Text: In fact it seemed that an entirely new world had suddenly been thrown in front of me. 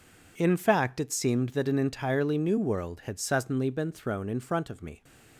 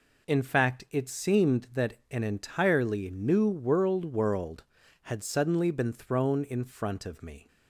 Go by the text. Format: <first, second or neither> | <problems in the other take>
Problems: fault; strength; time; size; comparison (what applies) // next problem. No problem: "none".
first | pauses between "that" and "an"; slight; at 1.9 s; 0.18 s long // says "world" twice; at 4.0 s